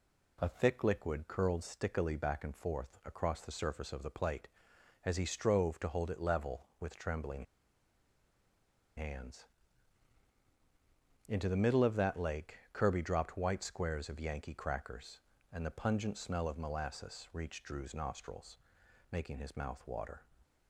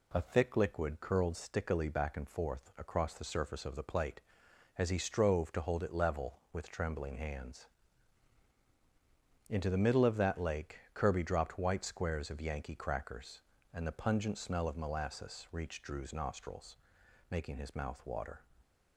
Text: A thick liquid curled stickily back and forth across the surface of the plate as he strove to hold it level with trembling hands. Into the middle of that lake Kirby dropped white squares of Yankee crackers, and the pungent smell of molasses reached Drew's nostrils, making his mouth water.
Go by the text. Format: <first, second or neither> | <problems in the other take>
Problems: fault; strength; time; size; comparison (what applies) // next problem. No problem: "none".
second | pauses between "trembling" and "hands"; strong; at 7.4 s; 1.5 s long